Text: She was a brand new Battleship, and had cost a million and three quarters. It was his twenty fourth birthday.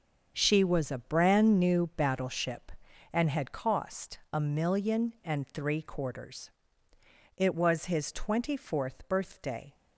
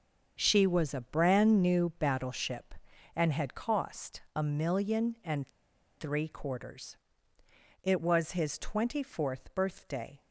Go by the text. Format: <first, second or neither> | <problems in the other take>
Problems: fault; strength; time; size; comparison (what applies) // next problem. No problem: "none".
first | starts louder than the rest; until 1.4 s; 7 dB; also in the first // pauses between "and" and "three"; noticeable; at 5.4 s; 0.49 s long